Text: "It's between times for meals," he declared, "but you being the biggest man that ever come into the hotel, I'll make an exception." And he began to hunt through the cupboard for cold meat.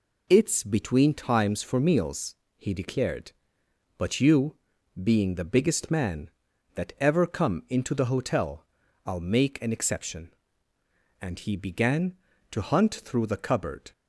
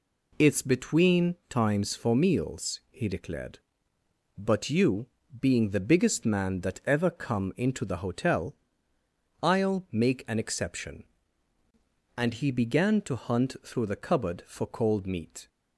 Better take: second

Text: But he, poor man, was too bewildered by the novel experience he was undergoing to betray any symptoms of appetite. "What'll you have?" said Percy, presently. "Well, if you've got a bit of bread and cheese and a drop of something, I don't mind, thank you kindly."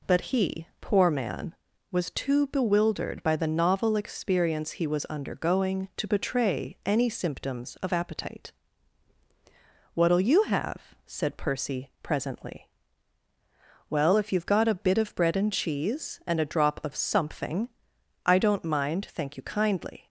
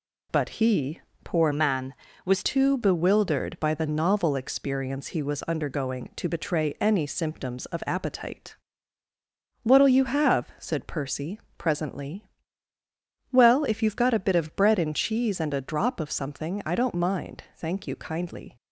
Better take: first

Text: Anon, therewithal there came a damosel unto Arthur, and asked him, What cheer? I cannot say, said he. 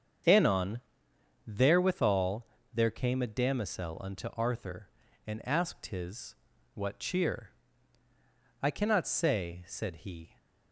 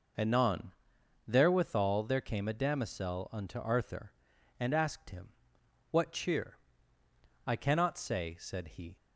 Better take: second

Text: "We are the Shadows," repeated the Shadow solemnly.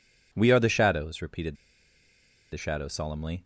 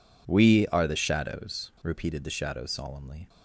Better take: second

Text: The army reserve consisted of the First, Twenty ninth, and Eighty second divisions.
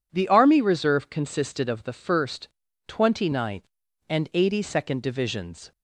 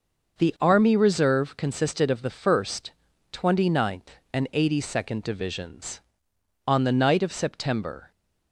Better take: first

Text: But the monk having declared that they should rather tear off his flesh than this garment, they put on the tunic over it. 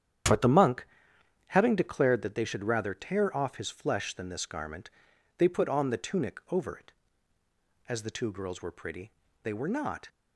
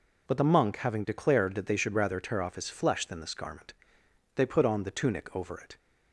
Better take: second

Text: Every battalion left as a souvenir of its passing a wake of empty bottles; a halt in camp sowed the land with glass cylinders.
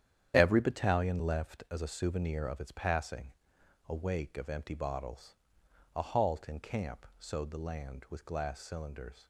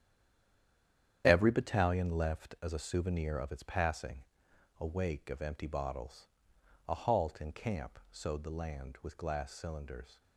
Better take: first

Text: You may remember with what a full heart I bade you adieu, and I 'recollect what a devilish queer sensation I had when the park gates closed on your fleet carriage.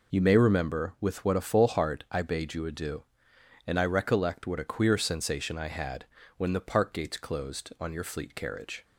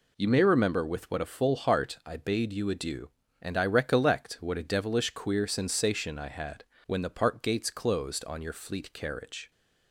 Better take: second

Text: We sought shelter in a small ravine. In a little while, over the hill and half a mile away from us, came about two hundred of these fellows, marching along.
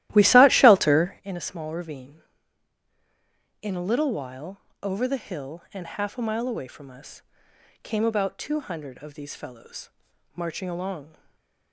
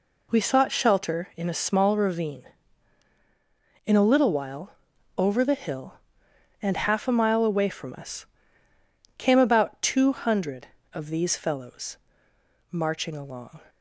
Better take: second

